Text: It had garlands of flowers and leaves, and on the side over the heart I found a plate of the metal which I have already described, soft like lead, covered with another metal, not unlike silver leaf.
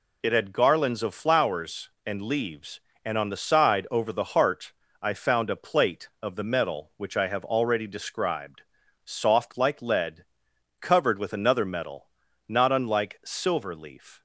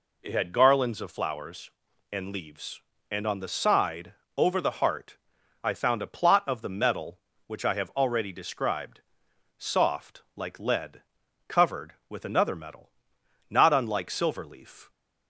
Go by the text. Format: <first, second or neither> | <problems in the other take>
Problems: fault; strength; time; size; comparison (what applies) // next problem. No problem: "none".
first | pauses between "side" and "over"; slight; at 4.1 s; 0.24 s long // pauses between "heart" and "I"; noticeable; at 5.1 s; 0.48 s long; slight in the first // says "plot" for "plate"; at 6.0 s